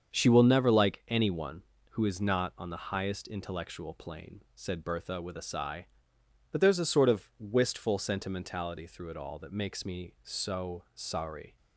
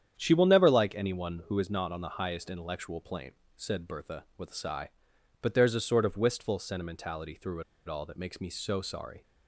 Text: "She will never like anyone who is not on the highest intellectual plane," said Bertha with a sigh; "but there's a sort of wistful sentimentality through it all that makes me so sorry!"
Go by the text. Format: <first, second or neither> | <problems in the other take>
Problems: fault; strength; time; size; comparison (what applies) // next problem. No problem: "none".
first | starts louder than the rest; strong; until 1.1 s; 9 dB; also in the first // pauses between "through" and "it"; slight; at 7.6 s; 0.25 s long